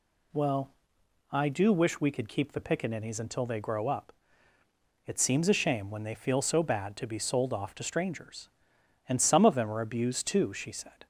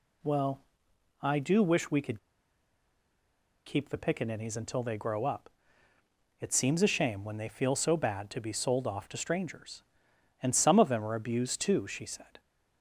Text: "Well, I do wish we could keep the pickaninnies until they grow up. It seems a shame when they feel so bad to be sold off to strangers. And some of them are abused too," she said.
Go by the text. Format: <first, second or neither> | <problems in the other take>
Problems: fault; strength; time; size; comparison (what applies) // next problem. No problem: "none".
first | pauses between "could" and "keep"; strong; at 2.1 s; 1.4 s long